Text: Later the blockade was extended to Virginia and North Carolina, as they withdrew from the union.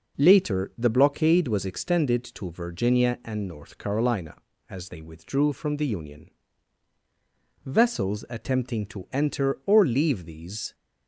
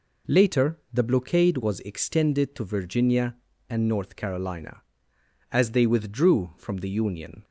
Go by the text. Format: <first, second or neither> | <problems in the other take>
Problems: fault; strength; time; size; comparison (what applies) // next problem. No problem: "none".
second | goes on to say "Vessels attempting to enter or leave these"; strong; from 7.6 s on; 3.1 s long